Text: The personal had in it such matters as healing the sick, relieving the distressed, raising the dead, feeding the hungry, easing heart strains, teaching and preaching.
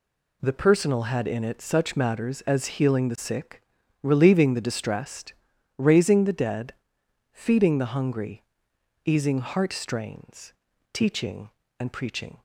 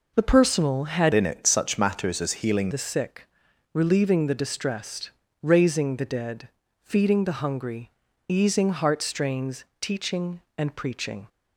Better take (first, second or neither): first